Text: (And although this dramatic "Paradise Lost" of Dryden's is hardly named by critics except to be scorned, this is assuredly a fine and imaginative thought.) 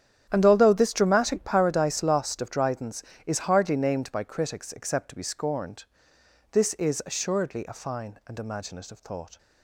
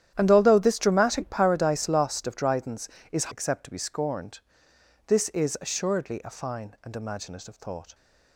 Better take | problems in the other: first | starts louder than the rest; strong; until 1.1 s; 10.5 dB; strong in the first // skips "hardly named by critics"; at 3.3 s

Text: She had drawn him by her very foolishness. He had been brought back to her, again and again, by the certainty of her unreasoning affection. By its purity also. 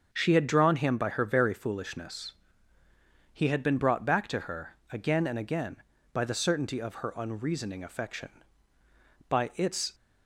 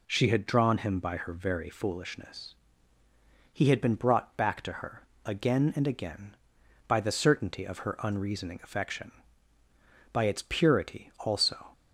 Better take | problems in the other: second | starts louder than the rest; until 1.1 s; 7 dB // stops before "purity also"; at 9.9 s

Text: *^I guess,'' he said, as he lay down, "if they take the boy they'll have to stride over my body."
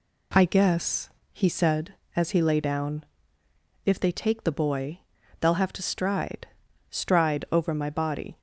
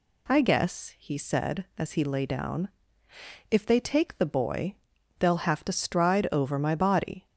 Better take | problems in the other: second | pauses between "boy" and "they'll"; at 5.0 s; 0.40 s long; noticeable in the second // says "stride" twice; at 6.9 s

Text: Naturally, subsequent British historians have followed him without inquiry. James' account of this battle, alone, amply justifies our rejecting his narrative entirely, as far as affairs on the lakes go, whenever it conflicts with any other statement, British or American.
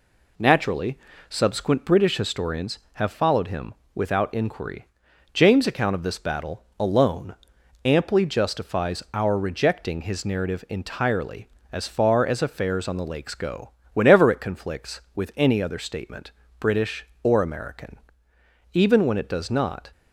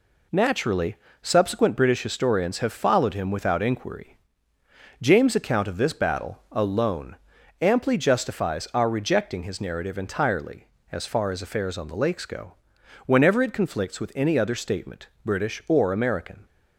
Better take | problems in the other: second | pauses between "him" and "without"; slight; at 3.7 s; 0.20 s long // goes on to say "Even when it does not"; noticeable; from 18.7 s on; 1.1 s long

